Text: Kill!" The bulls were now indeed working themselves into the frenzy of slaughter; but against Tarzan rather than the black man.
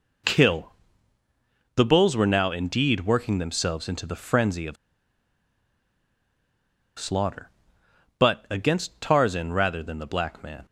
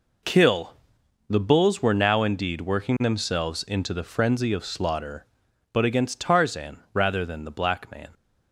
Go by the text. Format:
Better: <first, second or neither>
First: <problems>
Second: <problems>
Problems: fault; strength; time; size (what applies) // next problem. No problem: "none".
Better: second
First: pauses between "of" and "slaughter"; strong; at 4.7 s; 2.2 s long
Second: none